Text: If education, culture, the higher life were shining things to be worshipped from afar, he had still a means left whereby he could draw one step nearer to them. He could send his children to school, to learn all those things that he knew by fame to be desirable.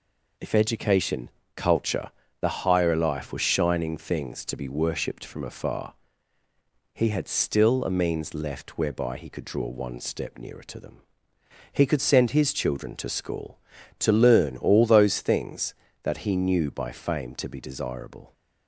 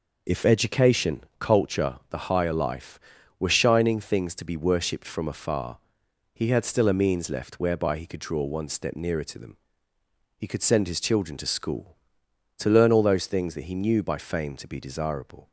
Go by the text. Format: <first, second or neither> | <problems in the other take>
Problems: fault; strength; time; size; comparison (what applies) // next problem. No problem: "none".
neither | none